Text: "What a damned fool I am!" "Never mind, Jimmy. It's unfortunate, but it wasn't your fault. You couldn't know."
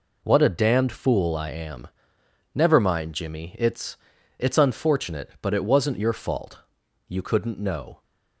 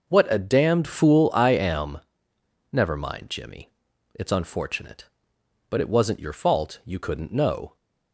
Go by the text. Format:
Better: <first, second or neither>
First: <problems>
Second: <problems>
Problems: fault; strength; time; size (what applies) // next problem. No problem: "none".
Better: second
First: says "It's" twice; at 4.3 s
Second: none